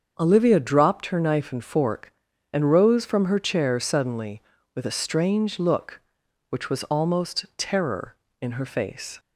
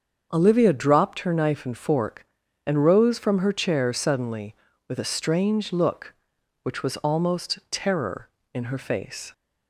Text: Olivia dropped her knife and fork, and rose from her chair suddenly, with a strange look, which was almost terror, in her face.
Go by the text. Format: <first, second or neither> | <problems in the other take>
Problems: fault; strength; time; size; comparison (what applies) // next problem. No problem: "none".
neither | starts louder than the rest; the same in both